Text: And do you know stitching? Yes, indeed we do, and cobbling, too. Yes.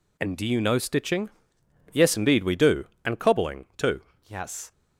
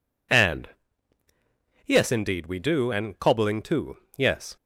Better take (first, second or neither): first